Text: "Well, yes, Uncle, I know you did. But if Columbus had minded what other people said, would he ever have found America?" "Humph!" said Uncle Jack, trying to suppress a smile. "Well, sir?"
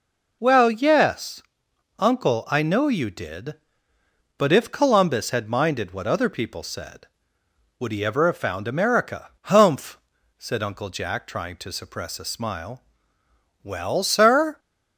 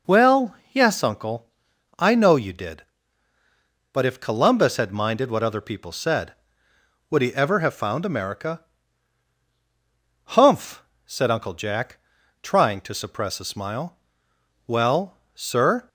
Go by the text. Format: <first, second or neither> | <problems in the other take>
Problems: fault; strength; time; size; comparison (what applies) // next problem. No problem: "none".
neither | none